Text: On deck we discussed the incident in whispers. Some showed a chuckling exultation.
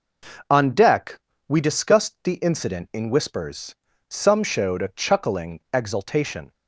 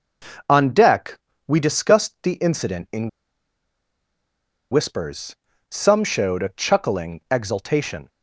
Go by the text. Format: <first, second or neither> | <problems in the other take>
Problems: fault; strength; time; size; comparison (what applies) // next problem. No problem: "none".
first | pauses between "deck" and "we"; slight; at 1.1 s; 0.30 s long; slight in the first // pauses between "in" and "whispers"; strong; at 3.0 s; 1.6 s long